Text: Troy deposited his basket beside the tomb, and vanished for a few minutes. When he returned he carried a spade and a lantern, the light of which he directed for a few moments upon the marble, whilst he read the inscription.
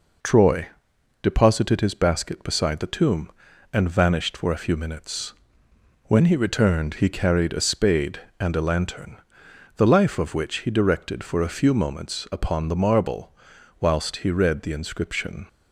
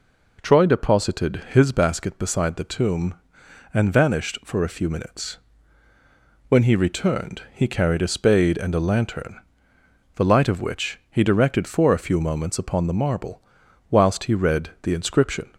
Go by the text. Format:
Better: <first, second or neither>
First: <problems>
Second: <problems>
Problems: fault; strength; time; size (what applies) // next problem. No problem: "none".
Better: second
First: pauses between "Troy" and "deposited"; noticeable; at 0.6 s; 0.56 s long // says "life" for "light"; at 9.8 s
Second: none